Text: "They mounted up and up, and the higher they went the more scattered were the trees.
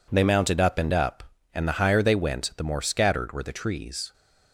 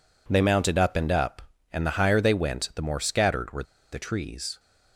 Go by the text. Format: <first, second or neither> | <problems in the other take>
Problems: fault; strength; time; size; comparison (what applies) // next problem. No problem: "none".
first | pauses between "were" and "the"; slight; at 3.6 s; 0.29 s long